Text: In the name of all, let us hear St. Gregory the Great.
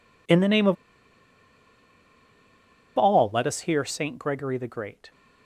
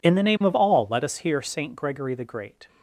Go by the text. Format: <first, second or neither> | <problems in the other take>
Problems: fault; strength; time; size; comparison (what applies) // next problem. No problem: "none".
second | pauses between "of" and "all"; strong; at 0.7 s; 2.2 s long